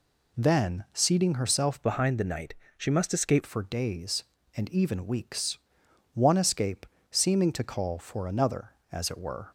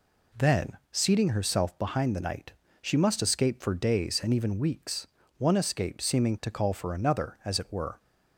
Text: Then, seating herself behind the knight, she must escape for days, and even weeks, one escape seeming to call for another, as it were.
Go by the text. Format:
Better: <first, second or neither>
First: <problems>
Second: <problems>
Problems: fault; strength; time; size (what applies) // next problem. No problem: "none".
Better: second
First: changes voice from "behind" to "escape"; from 1.8 to 3.4 s; 1.6 s long // pauses between "escape" and "seeming"; slight; at 6.8 s; 0.24 s long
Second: none